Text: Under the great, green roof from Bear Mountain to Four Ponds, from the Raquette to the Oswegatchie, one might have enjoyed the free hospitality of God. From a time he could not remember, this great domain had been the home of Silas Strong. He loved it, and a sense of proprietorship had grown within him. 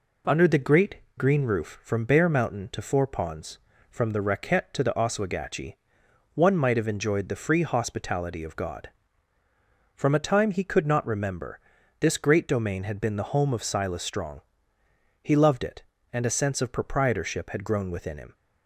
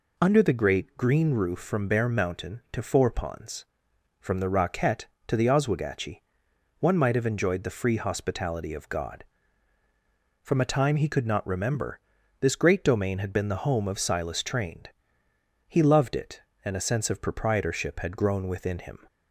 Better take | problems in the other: first | says "Trained" for "Strong"; at 14.4 s

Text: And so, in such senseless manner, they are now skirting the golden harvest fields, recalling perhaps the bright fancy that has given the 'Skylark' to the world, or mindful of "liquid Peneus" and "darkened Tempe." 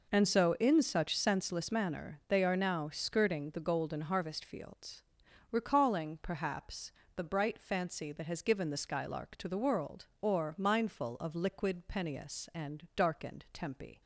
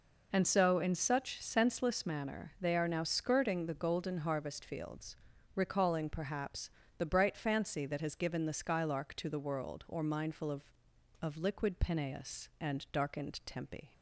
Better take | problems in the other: first | pauses between "perhaps" and "the"; slight; at 6.6 s; 0.30 s long; slight in the first // says "of" twice; at 11.1 s

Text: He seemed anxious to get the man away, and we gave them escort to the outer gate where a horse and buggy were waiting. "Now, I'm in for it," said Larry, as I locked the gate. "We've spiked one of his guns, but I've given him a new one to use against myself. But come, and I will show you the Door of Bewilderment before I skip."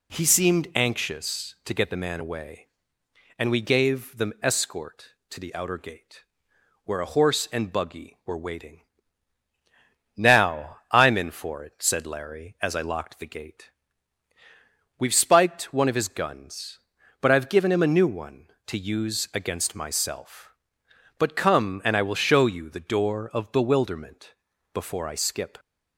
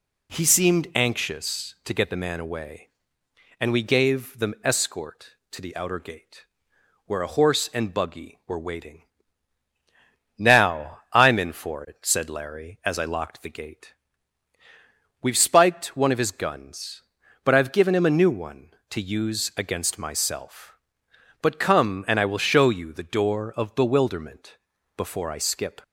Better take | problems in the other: neither | pauses between "gate" and "where"; noticeable; the same in both // pauses between "Bewilderment" and "before"; the same in both

